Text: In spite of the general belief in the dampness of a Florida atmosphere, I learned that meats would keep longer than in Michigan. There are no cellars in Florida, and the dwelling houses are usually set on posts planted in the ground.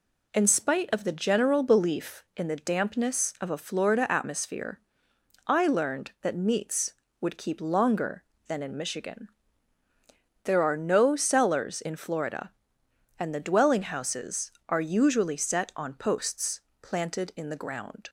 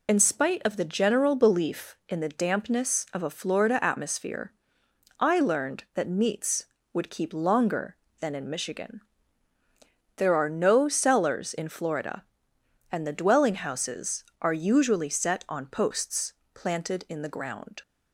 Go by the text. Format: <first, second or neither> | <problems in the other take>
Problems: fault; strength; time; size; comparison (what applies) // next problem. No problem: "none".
first | loses the start of "In"; at 0.0 s; 50 ms // pauses between "posts" and "planted"; slight; at 16.3 s; 0.24 s long; slight in the first